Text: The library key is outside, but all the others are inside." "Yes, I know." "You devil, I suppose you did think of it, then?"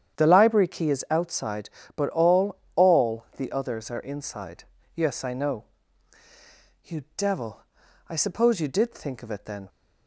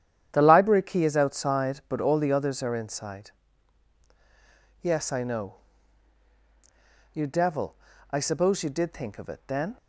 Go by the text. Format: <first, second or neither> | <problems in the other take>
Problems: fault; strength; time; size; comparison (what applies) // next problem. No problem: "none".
second | starts louder than the rest; strong; until 1.2 s; 9 dB; strong in the second // says "all" twice; at 2.7 s